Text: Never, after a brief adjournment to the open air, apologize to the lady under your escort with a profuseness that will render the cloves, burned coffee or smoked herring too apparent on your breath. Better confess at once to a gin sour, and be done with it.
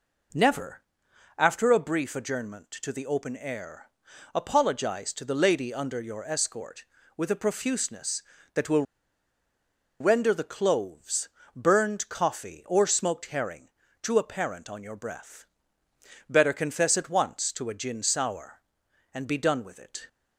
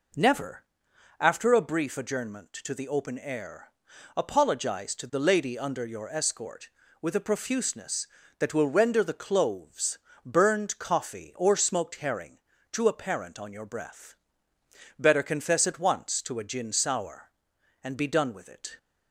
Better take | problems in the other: second | pauses between "will" and "render"; at 8.8 s; 1.1 s long // pauses between "herring" and "too"; slight; at 13.6 s; 0.34 s long; slight in the second

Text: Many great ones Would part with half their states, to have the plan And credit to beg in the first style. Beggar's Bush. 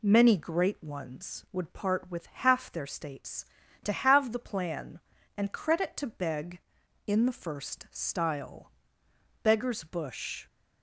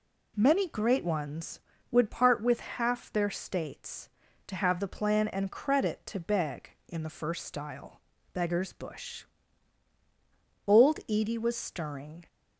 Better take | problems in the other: first | goes on to say "Old Edie was stirring"; from 10.6 s on; 1.6 s long

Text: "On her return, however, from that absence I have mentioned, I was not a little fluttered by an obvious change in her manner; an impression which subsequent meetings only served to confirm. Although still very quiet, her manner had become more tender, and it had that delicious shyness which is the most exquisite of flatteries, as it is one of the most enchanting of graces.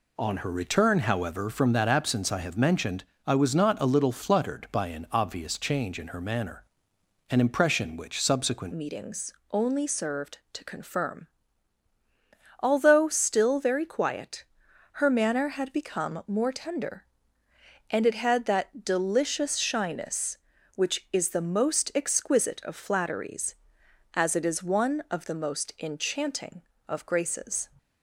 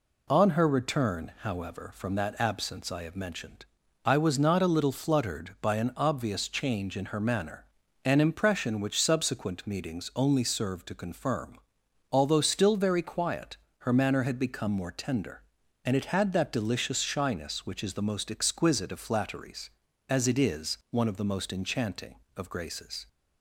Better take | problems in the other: second | changes voice at "meetings"; from 8.7 s on; 18.9 s long // pauses between "meetings" and "only"; slight; at 9.3 s; 0.16 s long

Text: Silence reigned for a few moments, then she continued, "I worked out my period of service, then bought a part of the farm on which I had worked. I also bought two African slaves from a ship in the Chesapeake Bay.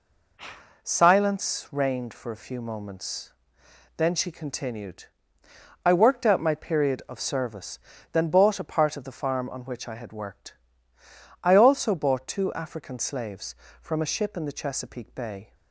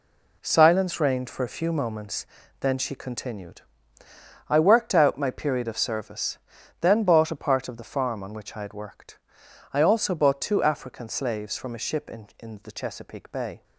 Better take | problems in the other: first | says "in" twice; at 12.3 s

